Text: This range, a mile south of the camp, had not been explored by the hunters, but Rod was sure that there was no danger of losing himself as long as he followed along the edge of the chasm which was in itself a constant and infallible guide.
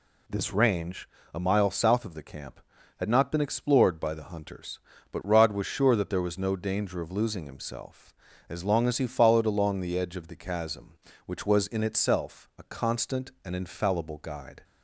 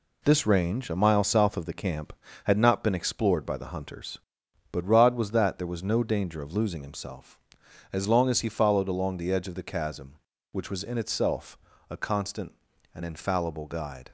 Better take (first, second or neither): first